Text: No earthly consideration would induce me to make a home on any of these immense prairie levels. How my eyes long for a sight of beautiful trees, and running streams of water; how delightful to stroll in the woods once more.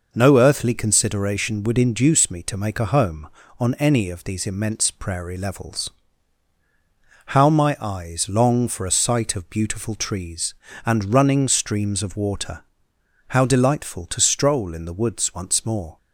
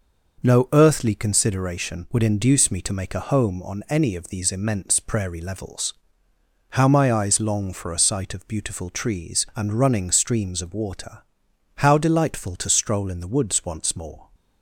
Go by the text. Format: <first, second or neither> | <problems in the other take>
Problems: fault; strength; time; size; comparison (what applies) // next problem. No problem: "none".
neither | none